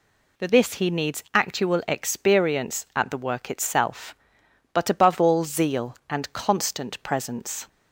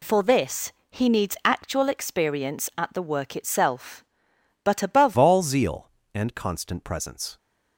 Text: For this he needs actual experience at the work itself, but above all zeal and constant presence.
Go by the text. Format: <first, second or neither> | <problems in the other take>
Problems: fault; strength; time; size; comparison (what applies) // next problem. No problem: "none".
first | pauses between "this" and "he"; slight; at 0.7 s; 0.18 s long // changes voice at "all"; from 5.1 s on; 2.2 s long